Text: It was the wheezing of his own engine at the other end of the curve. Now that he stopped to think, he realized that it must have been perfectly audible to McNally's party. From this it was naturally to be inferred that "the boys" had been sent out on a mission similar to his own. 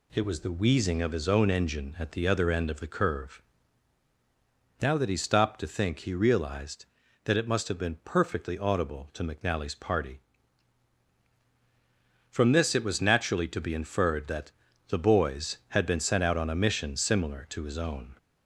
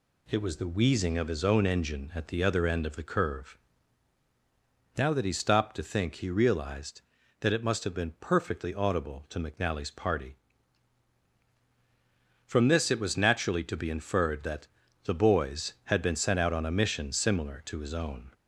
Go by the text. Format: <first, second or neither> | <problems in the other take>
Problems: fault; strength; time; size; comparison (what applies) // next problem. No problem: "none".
neither | pauses between "that" and "the"; the same in both